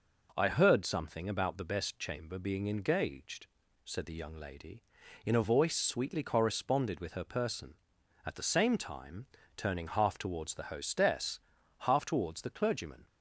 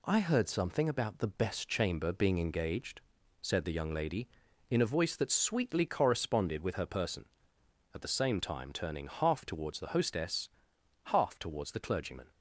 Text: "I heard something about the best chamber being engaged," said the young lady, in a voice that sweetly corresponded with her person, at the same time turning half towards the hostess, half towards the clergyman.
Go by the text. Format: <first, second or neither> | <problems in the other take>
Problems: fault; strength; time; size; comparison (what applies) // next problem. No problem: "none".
second | skips "that"; at 5.7 s // pauses between "time" and "turning"; slight; at 9.2 s; 0.30 s long